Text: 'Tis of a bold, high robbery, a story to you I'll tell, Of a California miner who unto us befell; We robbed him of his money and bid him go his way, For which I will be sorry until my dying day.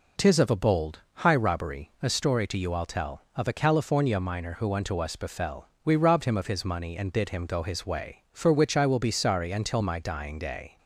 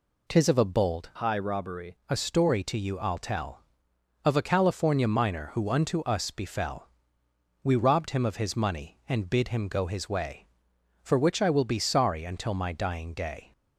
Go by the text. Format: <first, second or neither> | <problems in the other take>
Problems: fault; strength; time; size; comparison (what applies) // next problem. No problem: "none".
first | changes voice from "high" to "robbery"; from 1.1 to 1.9 s; 0.8 s long